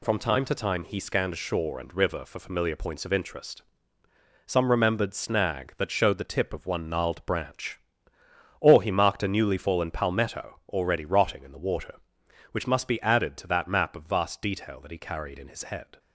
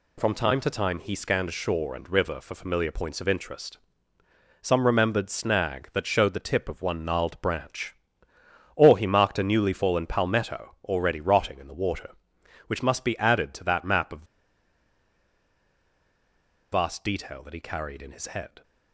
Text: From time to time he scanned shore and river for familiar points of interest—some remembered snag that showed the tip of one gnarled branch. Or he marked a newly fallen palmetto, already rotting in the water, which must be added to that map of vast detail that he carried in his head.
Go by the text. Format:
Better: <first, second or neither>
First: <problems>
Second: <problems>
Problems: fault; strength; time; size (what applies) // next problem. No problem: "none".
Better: first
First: none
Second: pauses between "of" and "vast"; strong; at 14.2 s; 2.4 s long